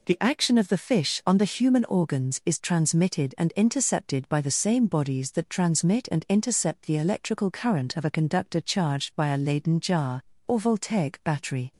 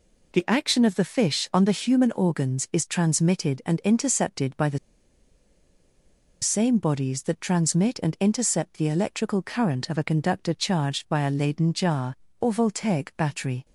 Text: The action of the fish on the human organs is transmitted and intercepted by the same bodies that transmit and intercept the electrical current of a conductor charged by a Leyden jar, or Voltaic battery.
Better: first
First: none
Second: pauses between "the" and "same"; strong; at 4.7 s; 1.6 s long

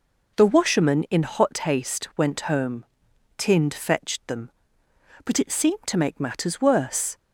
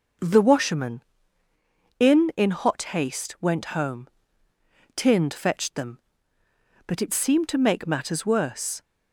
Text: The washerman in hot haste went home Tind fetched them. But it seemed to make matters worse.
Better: first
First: pauses between "home" and "Tind"; noticeable; at 2.8 s; 0.52 s long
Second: starts louder than the rest; noticeable; until 2.1 s; 6 dB // says "in" twice; at 2.3 s // pauses between "home" and "Tind"; noticeable; at 4.0 s; 0.88 s long

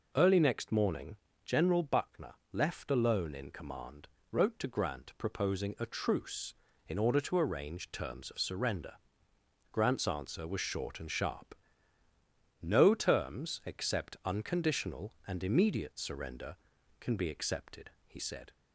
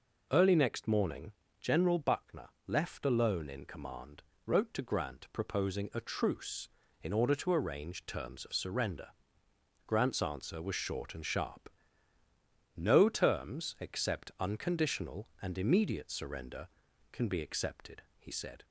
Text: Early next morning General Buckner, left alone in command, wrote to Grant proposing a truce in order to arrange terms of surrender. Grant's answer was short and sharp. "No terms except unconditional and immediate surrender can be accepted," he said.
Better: neither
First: pauses between "morning" and "General"; slight; at 1.1 s; 0.30 s long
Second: pauses between "morning" and "General"; slight; at 1.3 s; 0.30 s long

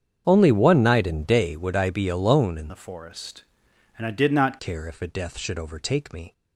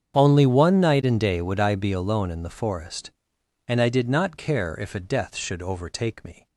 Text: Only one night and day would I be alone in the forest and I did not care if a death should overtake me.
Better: second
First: starts louder than the rest; strong; until 1.2 s; 8 dB // changes voice from "the" to "not"; from 2.6 to 4.5 s; 1.9 s long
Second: starts louder than the rest; strong; until 1.1 s; 7.5 dB

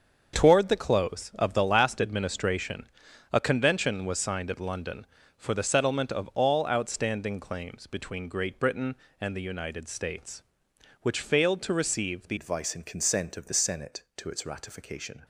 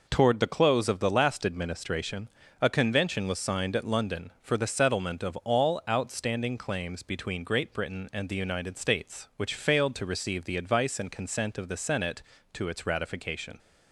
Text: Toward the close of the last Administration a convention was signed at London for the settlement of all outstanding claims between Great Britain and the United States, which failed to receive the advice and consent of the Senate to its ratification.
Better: second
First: starts louder than the rest; until 1.4 s; 7 dB // pauses between "Administration" and "a"; noticeable; at 2.8 s; 0.46 s long // changes voice at "advice"; from 12.3 s on; 2.9 s long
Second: pauses between "Administration" and "a"; slight; at 2.2 s; 0.29 s long

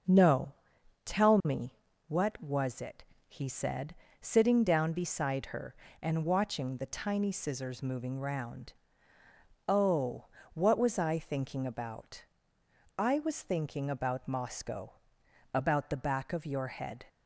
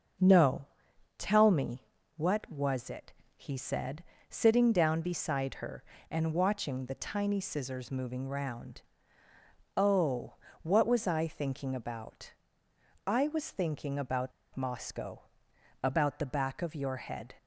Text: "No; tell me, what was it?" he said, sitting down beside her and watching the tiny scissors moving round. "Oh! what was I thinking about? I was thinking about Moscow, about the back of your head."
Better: first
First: starts louder than the rest; noticeable; until 1.6 s; 6 dB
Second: starts louder than the rest; noticeable; until 1.7 s; 6 dB // pauses between "about" and "Moscow"; slight; at 14.3 s; 0.23 s long

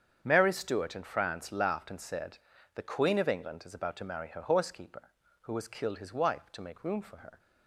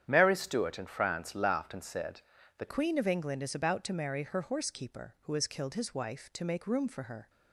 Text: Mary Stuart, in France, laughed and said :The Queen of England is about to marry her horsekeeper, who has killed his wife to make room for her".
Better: first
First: starts louder than the rest; strong; until 1.2 s; 7.5 dB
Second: starts louder than the rest; strong; until 1.0 s; 9.5 dB // changes voice at "Queen"; from 2.6 s on; 4.6 s long

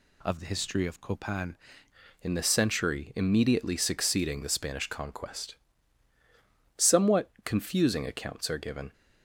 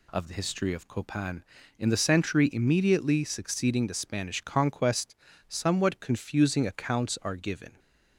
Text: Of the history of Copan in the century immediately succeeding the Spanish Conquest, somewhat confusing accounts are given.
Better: second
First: changes voice at "in"; from 2.2 s on; 6.7 s long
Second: none

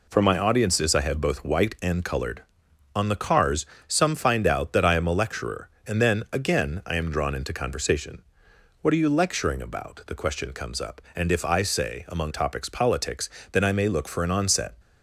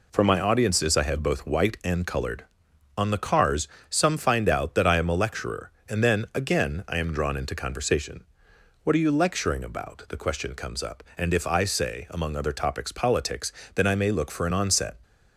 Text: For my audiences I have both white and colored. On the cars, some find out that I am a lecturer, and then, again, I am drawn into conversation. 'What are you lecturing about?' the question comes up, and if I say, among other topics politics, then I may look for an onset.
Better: second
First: skips "other"; at 12.3 s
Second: none

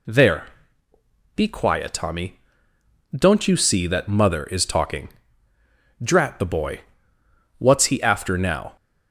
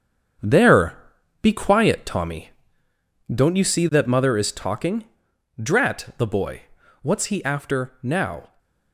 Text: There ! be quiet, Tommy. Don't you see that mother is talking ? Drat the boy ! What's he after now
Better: first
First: none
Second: gets quieter; strong; throughout; 8.5 dB

